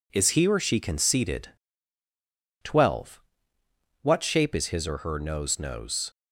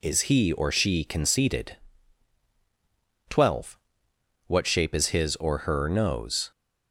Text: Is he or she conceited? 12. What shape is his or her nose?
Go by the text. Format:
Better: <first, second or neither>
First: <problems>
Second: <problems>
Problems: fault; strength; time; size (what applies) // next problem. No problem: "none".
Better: second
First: says "nose" twice; at 5.5 s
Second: none